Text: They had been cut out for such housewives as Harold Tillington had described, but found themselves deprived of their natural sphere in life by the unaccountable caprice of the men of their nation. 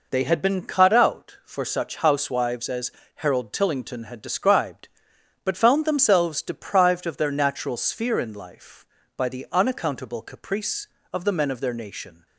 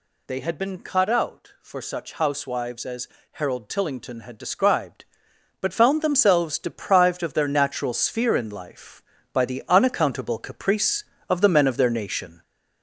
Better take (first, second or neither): first